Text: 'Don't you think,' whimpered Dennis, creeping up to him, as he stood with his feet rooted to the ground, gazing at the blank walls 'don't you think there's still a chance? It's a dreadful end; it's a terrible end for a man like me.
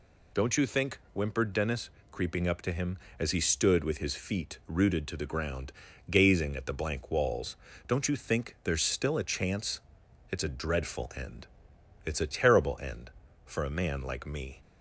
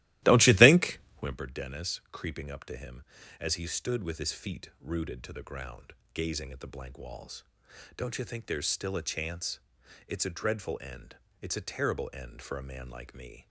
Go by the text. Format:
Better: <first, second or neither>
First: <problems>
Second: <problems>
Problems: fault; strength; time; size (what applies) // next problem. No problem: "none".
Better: first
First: pauses between "walls" and "don't"; slight; at 7.5 s; 0.32 s long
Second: starts louder than the rest; strong; until 1.4 s; 16 dB // pauses between "walls" and "don't"; noticeable; at 7.4 s; 0.52 s long